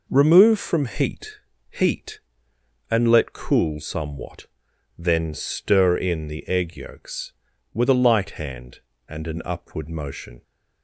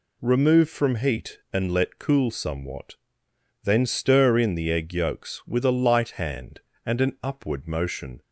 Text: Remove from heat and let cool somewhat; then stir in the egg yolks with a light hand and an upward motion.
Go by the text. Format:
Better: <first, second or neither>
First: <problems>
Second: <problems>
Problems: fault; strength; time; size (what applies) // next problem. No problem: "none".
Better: second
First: says "heat" twice; at 1.6 s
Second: none